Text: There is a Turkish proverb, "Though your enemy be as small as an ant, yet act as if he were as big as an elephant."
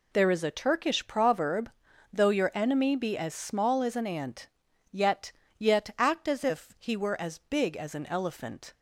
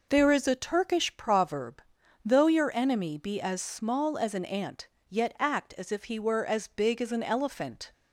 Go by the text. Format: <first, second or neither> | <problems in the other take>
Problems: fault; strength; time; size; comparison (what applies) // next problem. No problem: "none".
second | says "yet" twice; at 5.5 s